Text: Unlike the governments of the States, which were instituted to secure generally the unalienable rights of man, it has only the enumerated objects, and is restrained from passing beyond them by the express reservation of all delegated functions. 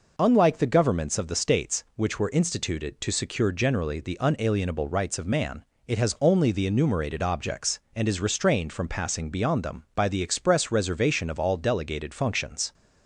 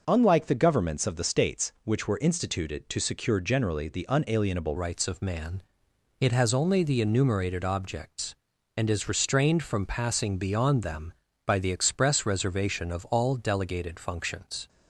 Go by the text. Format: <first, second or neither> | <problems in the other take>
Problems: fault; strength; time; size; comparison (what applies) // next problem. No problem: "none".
first | changes voice at "rights"; from 4.7 s on; 9.9 s long